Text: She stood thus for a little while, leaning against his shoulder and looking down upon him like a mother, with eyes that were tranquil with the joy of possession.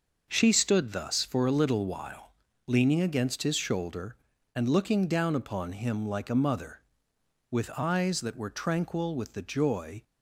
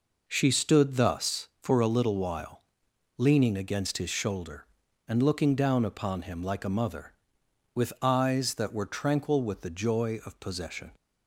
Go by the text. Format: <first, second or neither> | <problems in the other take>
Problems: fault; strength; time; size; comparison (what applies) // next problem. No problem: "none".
second | stops before "of possession"; at 10.0 s